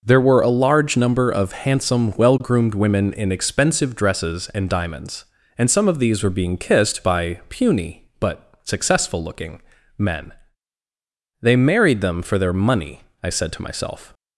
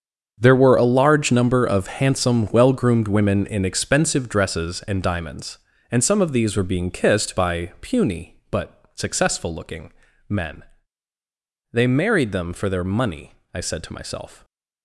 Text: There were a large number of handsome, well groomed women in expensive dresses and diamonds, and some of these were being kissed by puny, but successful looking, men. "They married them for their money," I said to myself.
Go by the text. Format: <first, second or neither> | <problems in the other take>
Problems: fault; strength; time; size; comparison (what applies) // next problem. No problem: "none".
first | gets quieter; strong; throughout; 13.5 dB